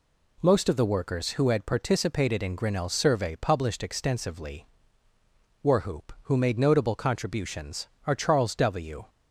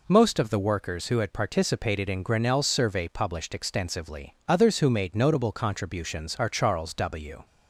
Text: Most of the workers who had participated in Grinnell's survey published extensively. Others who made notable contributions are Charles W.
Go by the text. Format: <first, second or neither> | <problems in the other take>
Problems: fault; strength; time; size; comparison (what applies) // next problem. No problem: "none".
second | says "Warhoop" for "Others"; at 5.6 s